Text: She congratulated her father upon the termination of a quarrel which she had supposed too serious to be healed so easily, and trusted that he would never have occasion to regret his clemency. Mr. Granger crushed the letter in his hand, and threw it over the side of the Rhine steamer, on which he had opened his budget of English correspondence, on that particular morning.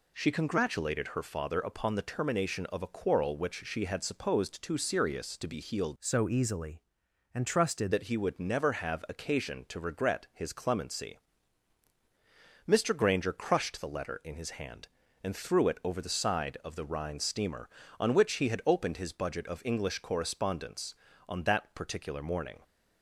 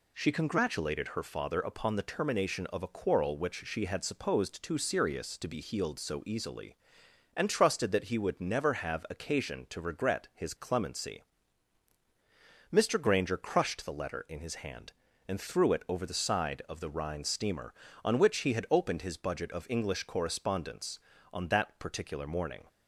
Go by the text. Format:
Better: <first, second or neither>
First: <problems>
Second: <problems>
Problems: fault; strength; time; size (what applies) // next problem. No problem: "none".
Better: second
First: changes voice from "so" to "trusted"; from 6.0 to 7.9 s; 1.9 s long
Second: none